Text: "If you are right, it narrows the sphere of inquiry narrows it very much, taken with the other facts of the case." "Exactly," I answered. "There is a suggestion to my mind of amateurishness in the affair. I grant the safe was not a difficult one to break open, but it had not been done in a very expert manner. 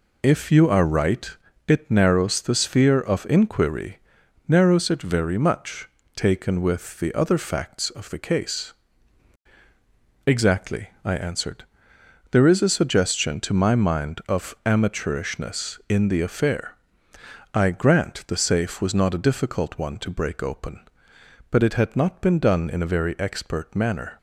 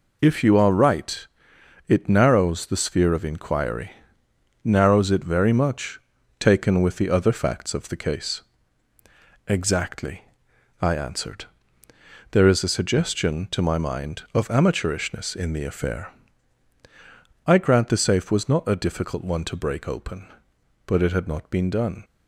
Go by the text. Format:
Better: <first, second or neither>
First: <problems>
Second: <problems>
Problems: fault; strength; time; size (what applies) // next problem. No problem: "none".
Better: first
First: pauses between "inquiry" and "narrows"; noticeable; at 3.9 s; 0.50 s long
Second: pauses between "inquiry" and "narrows"; noticeable; at 3.9 s; 0.70 s long // stops before "in a very expert manner"; at 22.0 s